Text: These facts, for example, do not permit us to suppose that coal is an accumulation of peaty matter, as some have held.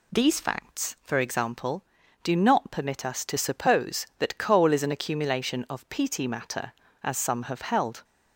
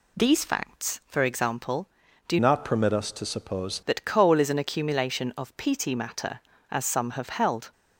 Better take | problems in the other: first | changes voice from "not" to "suppose"; from 2.3 to 3.8 s; 1.5 s long

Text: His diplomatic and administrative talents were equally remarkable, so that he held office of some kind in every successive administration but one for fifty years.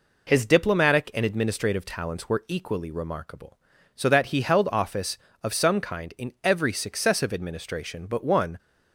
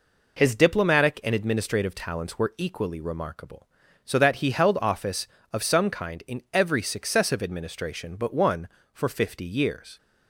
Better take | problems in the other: second | stops before "for fifty years"; at 8.5 s

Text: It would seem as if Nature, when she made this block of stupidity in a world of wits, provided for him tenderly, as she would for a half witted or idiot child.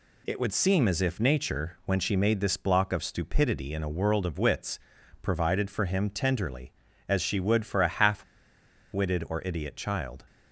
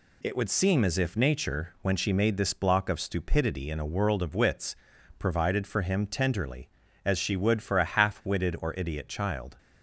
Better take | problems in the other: second | pauses between "half" and "witted"; noticeable; at 8.2 s; 0.68 s long

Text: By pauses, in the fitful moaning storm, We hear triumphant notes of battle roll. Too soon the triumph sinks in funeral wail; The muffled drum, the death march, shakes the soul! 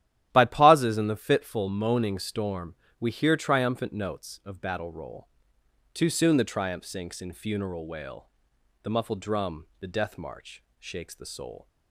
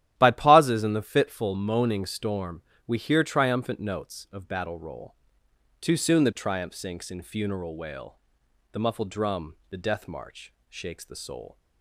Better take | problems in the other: neither | starts louder than the rest; strong; the same in both

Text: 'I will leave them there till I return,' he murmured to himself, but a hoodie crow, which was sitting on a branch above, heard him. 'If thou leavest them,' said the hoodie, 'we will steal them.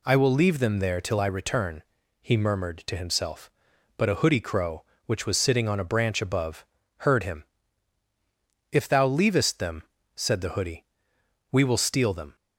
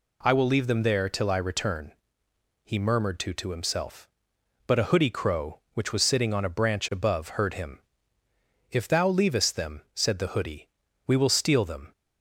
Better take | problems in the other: first | says "to" twice; at 3.3 s

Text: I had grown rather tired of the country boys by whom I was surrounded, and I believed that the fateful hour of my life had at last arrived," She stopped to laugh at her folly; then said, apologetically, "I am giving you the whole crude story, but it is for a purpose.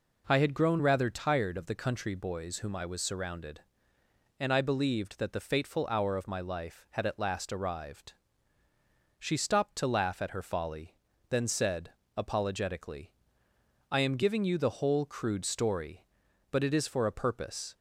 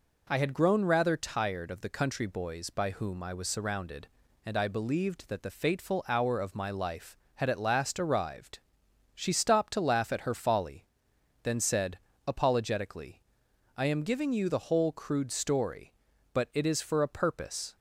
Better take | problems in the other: second | skips "by"; at 2.5 s

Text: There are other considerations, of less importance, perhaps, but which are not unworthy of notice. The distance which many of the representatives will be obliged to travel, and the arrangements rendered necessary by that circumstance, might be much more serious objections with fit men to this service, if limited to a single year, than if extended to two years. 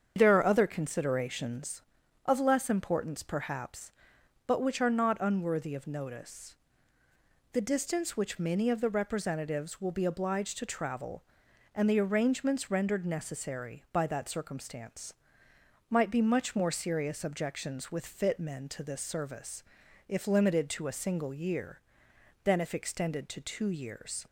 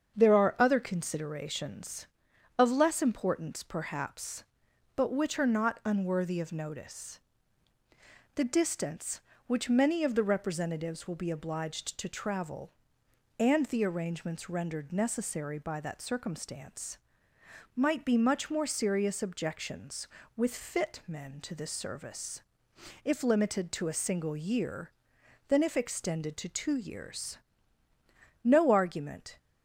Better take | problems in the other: first | starts louder than the rest; until 1.2 s; 7 dB; strong in the first // goes on to say "No argument"; noticeable; from 28.4 s on; 0.94 s long

